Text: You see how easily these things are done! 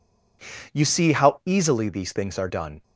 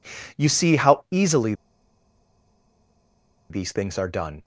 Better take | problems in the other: first | pauses between "easily" and "these"; strong; at 1.5 s; 1.9 s long

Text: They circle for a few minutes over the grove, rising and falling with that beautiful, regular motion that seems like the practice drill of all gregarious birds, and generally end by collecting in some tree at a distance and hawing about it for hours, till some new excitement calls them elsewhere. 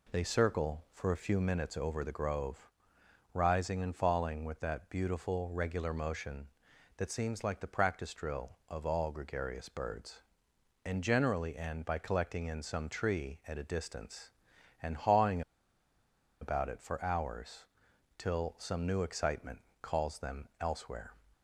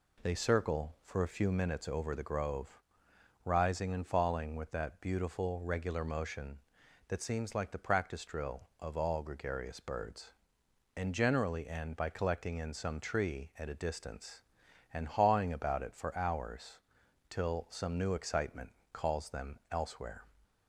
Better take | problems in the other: second | pauses between "hawing" and "about"; at 15.4 s; 0.99 s long // pauses between "excitement" and "calls"; slight; at 19.5 s; 0.24 s long; slight in the second

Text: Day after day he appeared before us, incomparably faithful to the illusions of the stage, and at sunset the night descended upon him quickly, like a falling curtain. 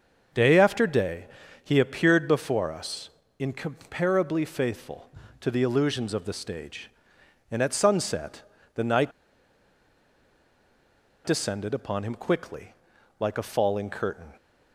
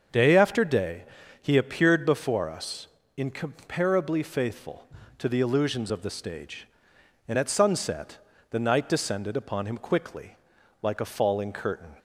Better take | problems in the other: second | starts louder than the rest; noticeable; until 1.7 s; 6 dB; also in the second // pauses between "day" and "he"; at 1.2 s; 0.38 s long; also in the second // pauses between "sunset" and "the"; slight; at 8.4 s; 0.32 s long; slight in the second // pauses between "night" and "descended"; strong; at 9.1 s; 2.1 s long

